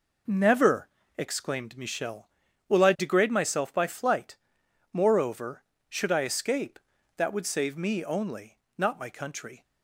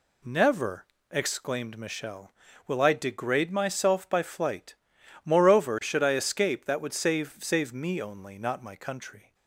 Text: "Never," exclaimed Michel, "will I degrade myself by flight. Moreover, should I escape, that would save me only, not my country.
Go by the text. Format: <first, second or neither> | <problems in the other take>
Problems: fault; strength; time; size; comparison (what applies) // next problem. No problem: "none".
first | says "save" twice; at 7.4 s